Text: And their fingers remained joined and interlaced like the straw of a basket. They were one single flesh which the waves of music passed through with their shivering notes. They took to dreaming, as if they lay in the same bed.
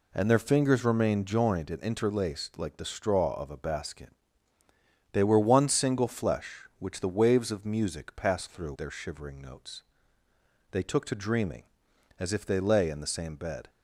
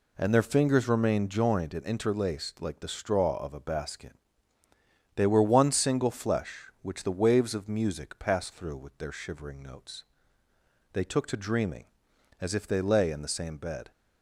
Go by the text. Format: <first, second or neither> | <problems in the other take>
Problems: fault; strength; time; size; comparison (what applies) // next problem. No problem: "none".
second | skips "with"; at 8.7 s